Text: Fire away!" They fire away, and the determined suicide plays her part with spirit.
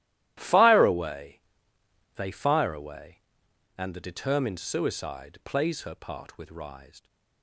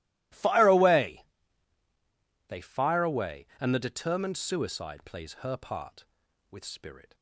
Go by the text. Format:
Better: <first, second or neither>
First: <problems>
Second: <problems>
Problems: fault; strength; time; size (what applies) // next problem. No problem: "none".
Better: second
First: starts louder than the rest; strong; until 1.3 s; 13.5 dB // says "rised" for "spirit"; at 6.5 s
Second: none